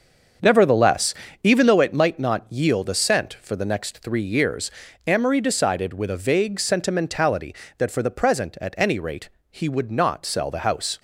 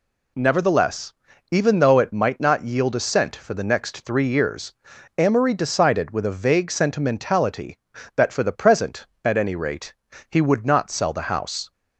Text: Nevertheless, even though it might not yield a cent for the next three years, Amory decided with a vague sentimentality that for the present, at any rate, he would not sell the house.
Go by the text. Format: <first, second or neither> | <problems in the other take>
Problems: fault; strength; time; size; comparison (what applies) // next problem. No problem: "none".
second | starts louder than the rest; until 2.1 s; 7 dB